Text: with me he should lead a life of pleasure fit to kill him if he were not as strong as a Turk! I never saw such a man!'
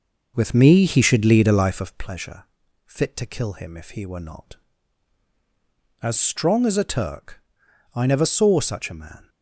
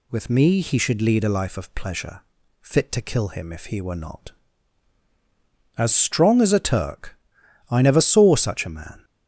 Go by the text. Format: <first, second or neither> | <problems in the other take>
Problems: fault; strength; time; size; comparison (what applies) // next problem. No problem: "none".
second | starts louder than the rest; noticeable; until 2.0 s; 6 dB // pauses between "pleasure" and "fit"; at 2.4 s; 0.42 s long; also in the second